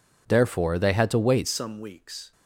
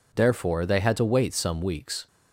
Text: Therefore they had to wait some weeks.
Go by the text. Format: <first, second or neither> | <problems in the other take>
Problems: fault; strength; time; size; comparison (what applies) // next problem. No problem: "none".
second | changes voice at "some"; from 1.4 s on; 0.9 s long